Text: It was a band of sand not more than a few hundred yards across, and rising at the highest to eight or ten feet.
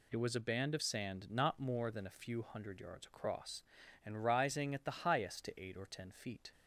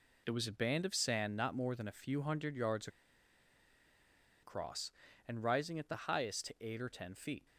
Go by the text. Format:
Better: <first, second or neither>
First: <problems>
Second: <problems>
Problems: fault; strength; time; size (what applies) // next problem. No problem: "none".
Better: first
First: none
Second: pauses between "yards" and "across"; strong; at 2.8 s; 1.5 s long